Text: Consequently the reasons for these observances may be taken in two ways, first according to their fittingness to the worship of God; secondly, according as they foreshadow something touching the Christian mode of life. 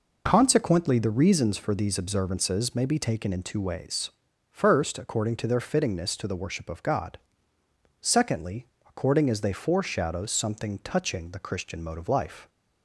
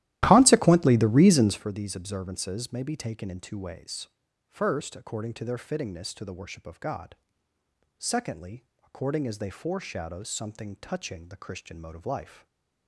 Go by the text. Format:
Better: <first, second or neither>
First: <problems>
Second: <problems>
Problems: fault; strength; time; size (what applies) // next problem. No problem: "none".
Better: first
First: none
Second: starts louder than the rest; strong; until 1.7 s; 14.5 dB // stays silent after the last word; slight; from 12.3 s on; 0.5 s long